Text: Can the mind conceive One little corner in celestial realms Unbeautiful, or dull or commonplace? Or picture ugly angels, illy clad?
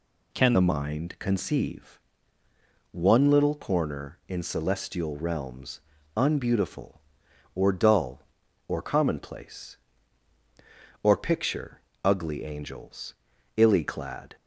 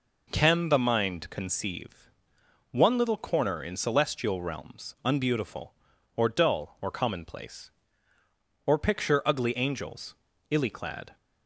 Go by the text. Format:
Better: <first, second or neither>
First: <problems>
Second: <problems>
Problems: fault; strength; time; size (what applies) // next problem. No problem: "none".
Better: second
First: changes voice at "the"; from 0.5 s on; 13.8 s long // pauses between "conceive" and "One"; noticeable; at 2.0 s; 0.90 s long // pauses between "realms" and "Unbeautiful"; at 5.7 s; 0.38 s long // pauses between "picture" and "ugly"; slight; at 11.7 s; 0.24 s long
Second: pauses between "conceive" and "One"; noticeable; at 2.0 s; 0.62 s long